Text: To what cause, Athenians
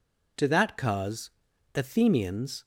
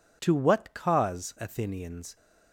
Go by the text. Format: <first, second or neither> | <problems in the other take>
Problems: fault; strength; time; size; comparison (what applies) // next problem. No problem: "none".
second | says "that" for "what"; at 0.4 s